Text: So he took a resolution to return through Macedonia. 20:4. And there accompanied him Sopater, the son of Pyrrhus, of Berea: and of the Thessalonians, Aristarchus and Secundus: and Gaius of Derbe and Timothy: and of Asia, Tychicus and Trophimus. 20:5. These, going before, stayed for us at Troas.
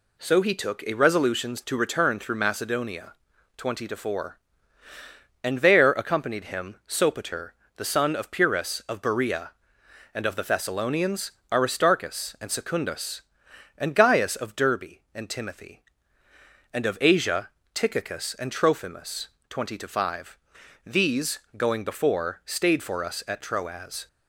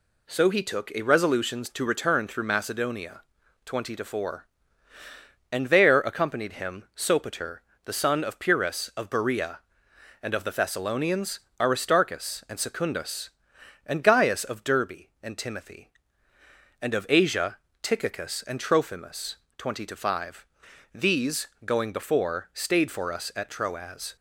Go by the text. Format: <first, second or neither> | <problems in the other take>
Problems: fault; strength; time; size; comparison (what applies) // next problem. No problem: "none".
neither | none